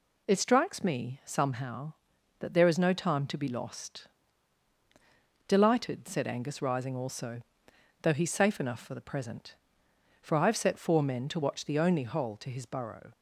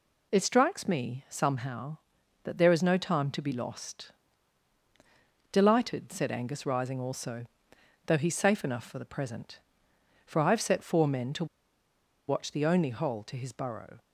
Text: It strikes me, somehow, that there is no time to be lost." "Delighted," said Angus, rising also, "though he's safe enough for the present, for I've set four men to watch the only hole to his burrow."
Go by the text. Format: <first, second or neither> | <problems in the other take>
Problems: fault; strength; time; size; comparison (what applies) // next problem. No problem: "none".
first | pauses between "to" and "watch"; noticeable; at 11.4 s; 0.83 s long